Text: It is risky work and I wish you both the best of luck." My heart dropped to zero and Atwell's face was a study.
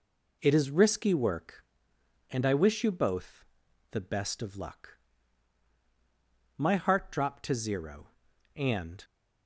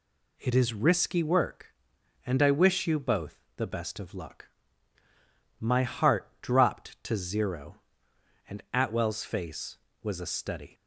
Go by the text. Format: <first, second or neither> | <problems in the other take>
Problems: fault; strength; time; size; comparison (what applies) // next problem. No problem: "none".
second | pauses between "both" and "the"; noticeable; at 3.4 s; 0.48 s long; slight in the second // stops before "Atwell's face was a study"; at 9.0 s